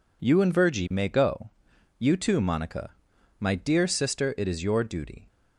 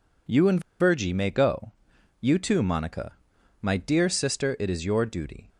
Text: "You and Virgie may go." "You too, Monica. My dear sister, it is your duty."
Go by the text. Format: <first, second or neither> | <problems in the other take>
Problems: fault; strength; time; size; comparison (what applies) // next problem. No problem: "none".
first | pauses between "and" and "Virgie"; slight; at 0.5 s; 0.20 s long